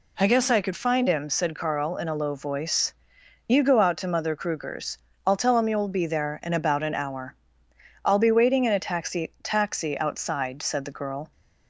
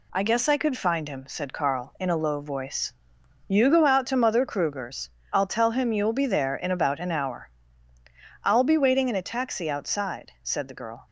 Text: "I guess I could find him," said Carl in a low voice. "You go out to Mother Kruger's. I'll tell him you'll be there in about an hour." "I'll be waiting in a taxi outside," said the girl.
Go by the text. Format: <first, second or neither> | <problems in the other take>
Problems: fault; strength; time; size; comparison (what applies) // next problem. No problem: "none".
second | says "taxi" twice; at 9.4 s